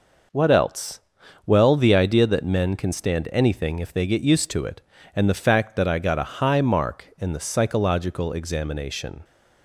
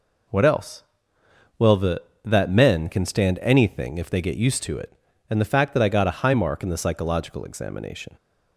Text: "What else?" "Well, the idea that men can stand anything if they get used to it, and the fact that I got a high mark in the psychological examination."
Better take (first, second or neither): first